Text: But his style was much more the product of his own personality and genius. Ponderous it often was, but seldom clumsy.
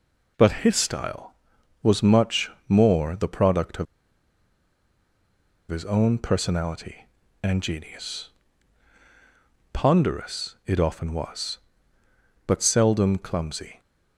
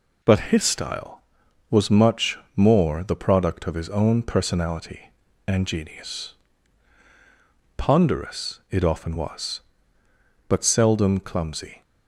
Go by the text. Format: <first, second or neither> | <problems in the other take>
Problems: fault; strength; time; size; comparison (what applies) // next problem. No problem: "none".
second | pauses between "much" and "more"; slight; at 2.5 s; 0.16 s long; slight in the second // pauses between "of" and "his"; strong; at 3.8 s; 1.8 s long